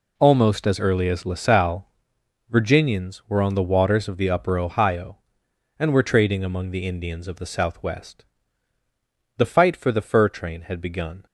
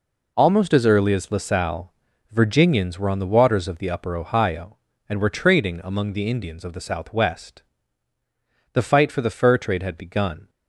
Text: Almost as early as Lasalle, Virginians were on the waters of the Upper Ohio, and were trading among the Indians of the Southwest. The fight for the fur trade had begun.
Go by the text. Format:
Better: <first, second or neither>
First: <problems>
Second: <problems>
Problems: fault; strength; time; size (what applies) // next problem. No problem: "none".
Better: second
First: says "train" for "trade"; at 10.2 s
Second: none